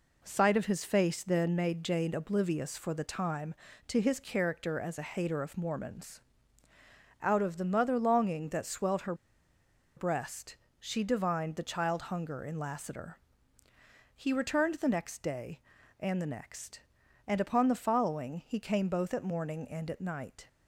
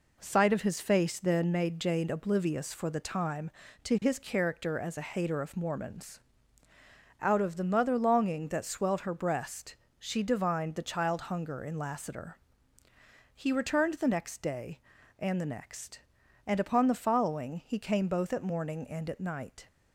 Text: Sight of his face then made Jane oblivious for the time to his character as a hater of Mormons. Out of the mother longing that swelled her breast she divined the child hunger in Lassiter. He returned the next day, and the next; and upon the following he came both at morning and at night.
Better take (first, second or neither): second